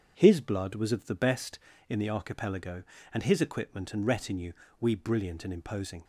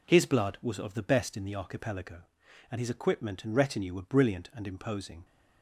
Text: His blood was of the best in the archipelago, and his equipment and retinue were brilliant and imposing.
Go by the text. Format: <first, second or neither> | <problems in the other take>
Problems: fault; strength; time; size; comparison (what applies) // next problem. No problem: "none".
second | says "we" for "were"; at 4.7 s